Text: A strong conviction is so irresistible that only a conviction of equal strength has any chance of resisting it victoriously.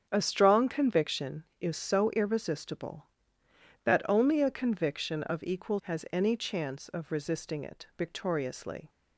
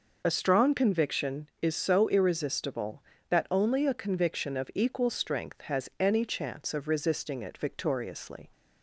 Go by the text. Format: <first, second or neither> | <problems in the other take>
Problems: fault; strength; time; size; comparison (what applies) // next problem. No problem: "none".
second | starts louder than the rest; strong; until 1.1 s; 7.5 dB // skips "strength"; at 5.8 s